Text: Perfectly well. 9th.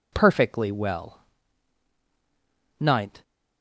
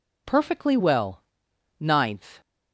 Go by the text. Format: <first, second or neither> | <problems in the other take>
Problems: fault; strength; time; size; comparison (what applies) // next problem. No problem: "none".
neither | none